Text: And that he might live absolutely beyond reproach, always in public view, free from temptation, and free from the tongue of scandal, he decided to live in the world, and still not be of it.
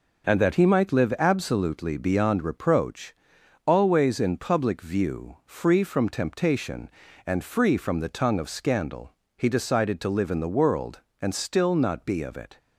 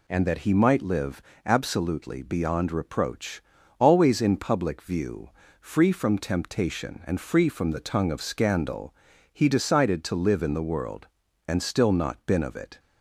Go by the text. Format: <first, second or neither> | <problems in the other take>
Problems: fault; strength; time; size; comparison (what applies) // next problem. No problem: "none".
first | pauses between "live" and "absolutely"; slight; at 1.2 s; 0.24 s long // says "been" for "be"; at 12.2 s